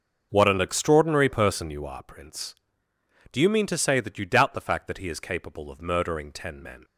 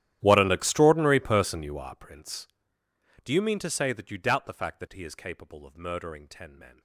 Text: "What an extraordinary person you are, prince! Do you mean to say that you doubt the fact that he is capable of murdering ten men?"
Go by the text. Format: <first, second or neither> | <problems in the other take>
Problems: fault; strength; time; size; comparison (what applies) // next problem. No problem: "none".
first | gets quieter; strong; throughout; 23 dB // starts louder than the rest; strong; until 1.2 s; 12 dB; also in the first